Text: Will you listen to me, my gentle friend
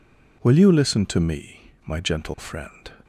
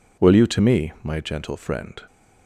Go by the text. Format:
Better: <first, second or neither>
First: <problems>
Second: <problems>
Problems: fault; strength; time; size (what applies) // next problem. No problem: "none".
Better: first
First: none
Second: skips "listen"; at 0.4 s